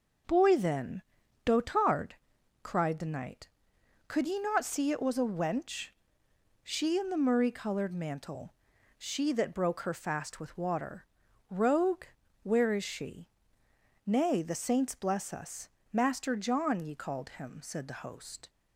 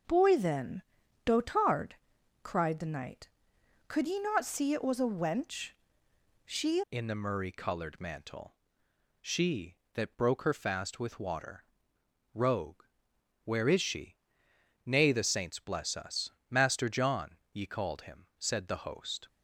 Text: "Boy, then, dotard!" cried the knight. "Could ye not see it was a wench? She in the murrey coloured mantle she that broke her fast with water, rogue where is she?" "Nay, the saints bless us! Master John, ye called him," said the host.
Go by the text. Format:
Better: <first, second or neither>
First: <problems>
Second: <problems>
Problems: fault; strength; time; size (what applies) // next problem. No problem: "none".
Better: first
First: pauses between "mantle" and "she"; noticeable; at 8.5 s; 0.46 s long // pauses between "rogue" and "where"; at 12.0 s; 0.38 s long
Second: changes voice at "in"; from 6.9 s on; 12.3 s long // pauses between "mantle" and "she"; noticeable; at 8.5 s; 0.66 s long // pauses between "rogue" and "where"; noticeable; at 12.8 s; 0.58 s long